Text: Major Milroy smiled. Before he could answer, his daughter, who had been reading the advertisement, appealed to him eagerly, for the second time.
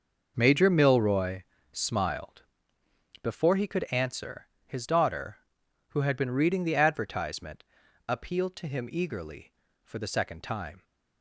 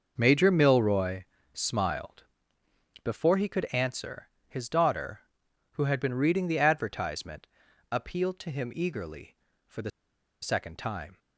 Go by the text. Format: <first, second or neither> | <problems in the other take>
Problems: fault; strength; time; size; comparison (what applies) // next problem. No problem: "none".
first | starts louder than the rest; noticeable; until 1.1 s; 6 dB // pauses between "Milroy" and "smiled"; slight; at 1.2 s; 0.28 s long; slight in the first // pauses between "the" and "second"; noticeable; at 9.9 s; 0.52 s long